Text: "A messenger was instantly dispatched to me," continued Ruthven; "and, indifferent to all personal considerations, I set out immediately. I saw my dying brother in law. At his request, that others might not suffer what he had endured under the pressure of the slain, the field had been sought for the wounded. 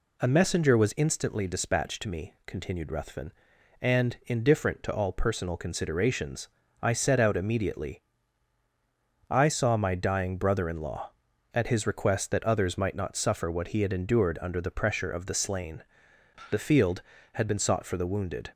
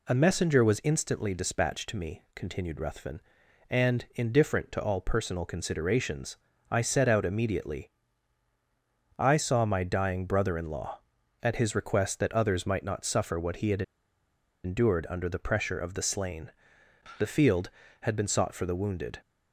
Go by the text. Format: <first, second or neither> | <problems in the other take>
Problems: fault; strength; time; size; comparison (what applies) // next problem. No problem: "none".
first | pauses between "had" and "endured"; noticeable; at 13.8 s; 0.82 s long